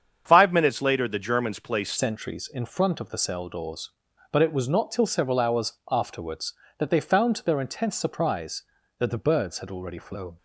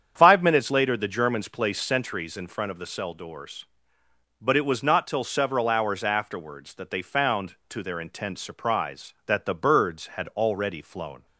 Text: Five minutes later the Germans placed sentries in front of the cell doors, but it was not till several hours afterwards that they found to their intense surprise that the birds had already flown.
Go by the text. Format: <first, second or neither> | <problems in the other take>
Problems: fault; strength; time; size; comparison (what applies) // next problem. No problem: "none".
second | starts louder than the rest; strong; until 1.2 s; 7.5 dB; strong in the second // changes voice at "sentries"; from 1.9 s on; 8.4 s long // pauses between "hours" and "afterwards"; slight; at 5.7 s; 0.16 s long